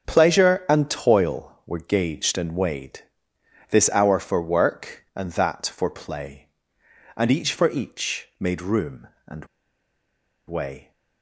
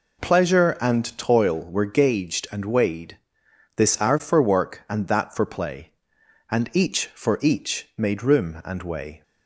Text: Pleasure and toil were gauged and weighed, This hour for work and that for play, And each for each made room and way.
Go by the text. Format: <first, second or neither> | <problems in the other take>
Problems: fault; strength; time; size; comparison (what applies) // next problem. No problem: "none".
second | starts louder than the rest; until 1.1 s; 6.5 dB // pauses between "and" and "way"; at 9.4 s; 1.0 s long